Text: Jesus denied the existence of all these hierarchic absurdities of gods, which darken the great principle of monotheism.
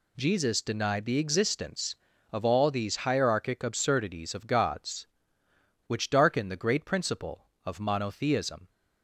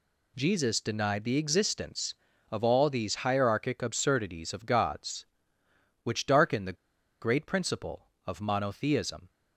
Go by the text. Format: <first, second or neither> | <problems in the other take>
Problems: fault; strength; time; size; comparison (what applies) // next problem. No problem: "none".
first | pauses between "the" and "great"; noticeable; at 6.7 s; 0.47 s long